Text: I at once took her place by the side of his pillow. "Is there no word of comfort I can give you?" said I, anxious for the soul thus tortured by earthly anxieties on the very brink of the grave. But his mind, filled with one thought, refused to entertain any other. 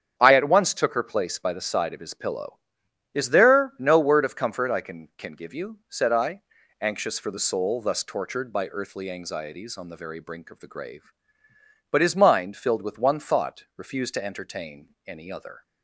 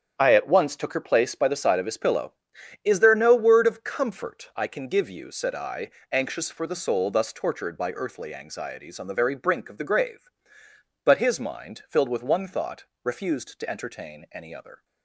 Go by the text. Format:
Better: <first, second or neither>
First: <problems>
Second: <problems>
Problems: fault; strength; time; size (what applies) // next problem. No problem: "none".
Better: second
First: starts louder than the rest; strong; until 1.2 s; 8 dB // says "can" twice; at 5.1 s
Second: starts louder than the rest; strong; until 1.1 s; 9 dB